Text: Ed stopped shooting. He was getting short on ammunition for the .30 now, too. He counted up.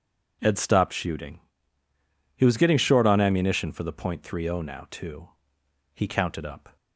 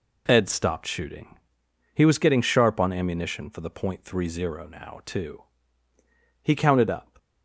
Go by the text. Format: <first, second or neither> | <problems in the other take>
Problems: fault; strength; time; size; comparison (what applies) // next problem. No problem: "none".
first | says "sharp" for "short"; at 2.4 s